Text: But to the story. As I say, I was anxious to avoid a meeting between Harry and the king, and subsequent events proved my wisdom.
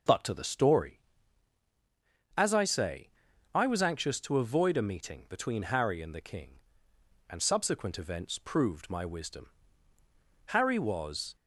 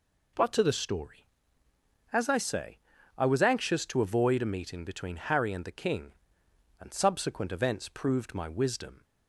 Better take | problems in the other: second | starts louder than the rest; until 2.4 s; 6 dB // goes on to say "Harry was"; noticeable; from 10.4 s on; 0.90 s long

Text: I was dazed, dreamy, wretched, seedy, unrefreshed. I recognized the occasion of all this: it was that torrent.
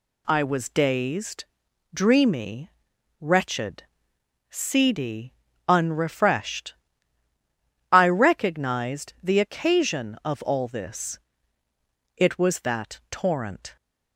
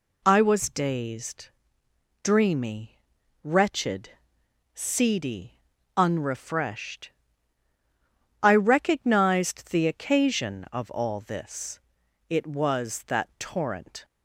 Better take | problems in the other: neither | none

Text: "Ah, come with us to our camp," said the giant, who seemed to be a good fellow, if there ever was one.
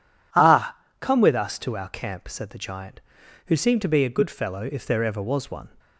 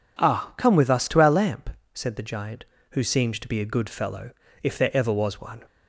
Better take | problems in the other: first | says "lamp" for "camp"; at 1.2 s

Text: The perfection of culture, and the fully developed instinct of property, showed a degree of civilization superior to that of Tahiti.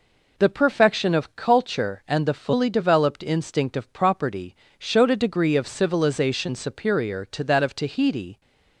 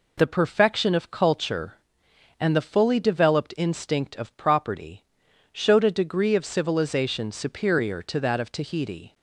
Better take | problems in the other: neither | none

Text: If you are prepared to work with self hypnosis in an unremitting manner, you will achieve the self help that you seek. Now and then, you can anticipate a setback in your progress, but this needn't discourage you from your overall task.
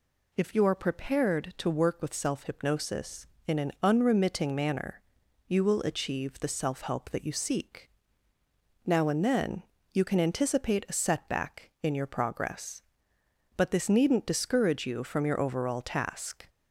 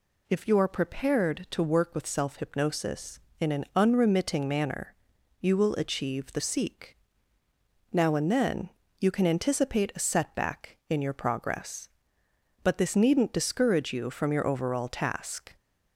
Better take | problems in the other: first | skips "self help that you"; at 6.4 s

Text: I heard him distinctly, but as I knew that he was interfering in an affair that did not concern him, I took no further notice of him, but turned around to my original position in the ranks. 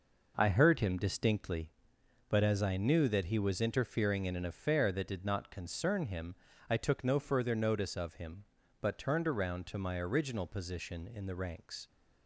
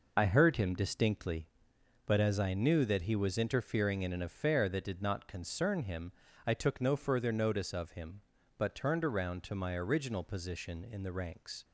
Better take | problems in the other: first | loses the start of "I"; at 0.1 s; 55 ms

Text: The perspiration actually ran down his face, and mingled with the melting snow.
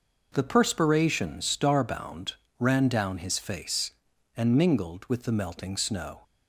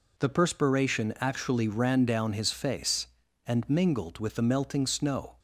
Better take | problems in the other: second | says "starbound" for "actually"; at 1.4 s

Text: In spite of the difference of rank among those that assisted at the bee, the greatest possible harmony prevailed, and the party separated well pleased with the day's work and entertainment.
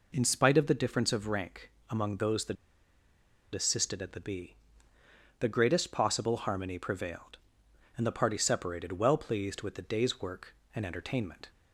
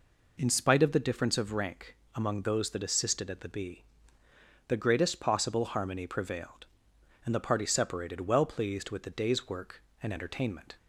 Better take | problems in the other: second | pauses between "rank" and "among"; slight; at 1.7 s; 0.18 s long; slight in the second // pauses between "that" and "assisted"; at 2.5 s; 0.98 s long

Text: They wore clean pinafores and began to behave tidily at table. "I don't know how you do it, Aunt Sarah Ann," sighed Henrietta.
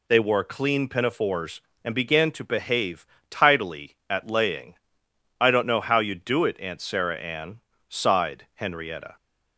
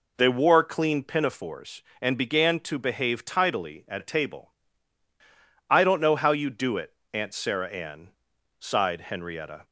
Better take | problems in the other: second | pauses between "behave" and "tidily"; slight; at 3.0 s; 0.24 s long // says "laying" for "table"; at 4.2 s

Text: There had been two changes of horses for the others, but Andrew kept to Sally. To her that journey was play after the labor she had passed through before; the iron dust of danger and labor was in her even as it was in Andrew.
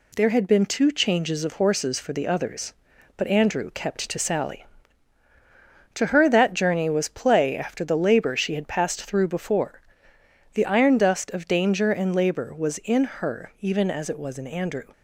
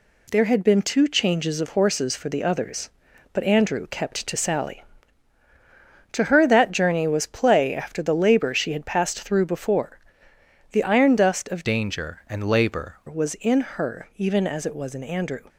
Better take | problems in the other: first | changes voice from "danger" to "labor"; from 11.6 to 12.9 s; 1.3 s long

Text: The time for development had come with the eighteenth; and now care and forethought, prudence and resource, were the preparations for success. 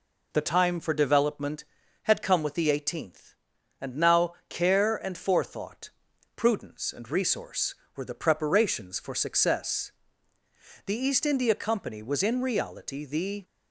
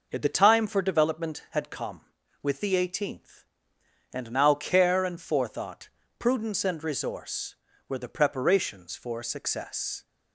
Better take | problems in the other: second | pauses between "now" and "care"; slight; at 4.3 s; 0.16 s long // goes on to say "The East India Company was in reality the"; strong; from 10.8 s on; 2.5 s long

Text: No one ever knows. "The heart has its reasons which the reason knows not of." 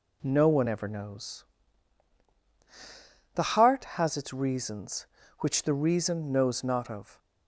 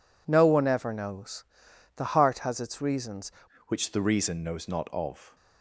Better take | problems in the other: first | changes voice at "which"; from 3.6 s on; 1.7 s long

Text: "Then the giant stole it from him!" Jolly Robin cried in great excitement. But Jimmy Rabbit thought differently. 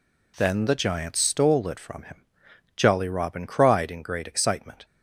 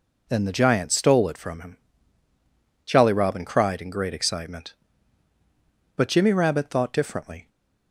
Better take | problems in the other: second | stops before "But Jimmy Rabbit thought differently"; at 4.8 s

